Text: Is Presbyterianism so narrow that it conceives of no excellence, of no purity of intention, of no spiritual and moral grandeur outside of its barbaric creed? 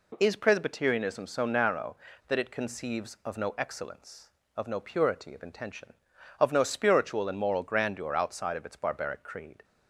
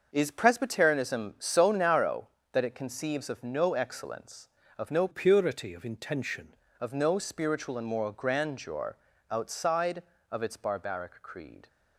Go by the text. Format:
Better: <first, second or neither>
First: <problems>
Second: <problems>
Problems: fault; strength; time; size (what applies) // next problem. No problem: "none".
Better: first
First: none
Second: starts louder than the rest; until 1.1 s; 6.5 dB // changes voice from "purity" to "intention"; from 5.1 to 6.5 s; 1.4 s long // pauses between "grandeur" and "outside"; slight; at 8.9 s; 0.34 s long